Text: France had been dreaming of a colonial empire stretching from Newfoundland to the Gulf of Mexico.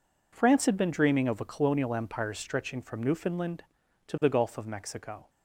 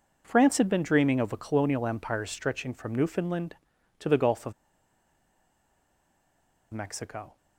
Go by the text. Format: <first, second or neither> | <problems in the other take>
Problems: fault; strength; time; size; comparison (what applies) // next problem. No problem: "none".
first | pauses between "of" and "Mexico"; strong; at 4.5 s; 2.2 s long